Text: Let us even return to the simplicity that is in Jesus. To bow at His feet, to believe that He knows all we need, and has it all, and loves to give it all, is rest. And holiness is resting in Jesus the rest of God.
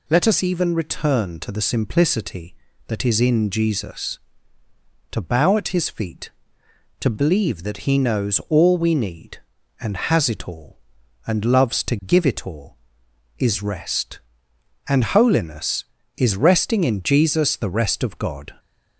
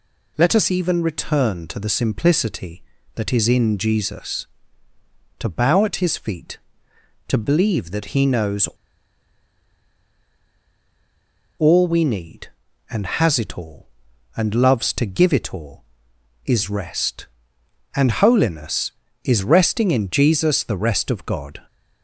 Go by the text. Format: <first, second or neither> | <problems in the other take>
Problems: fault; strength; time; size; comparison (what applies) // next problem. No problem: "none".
first | pauses between "knows" and "all"; strong; at 8.6 s; 2.9 s long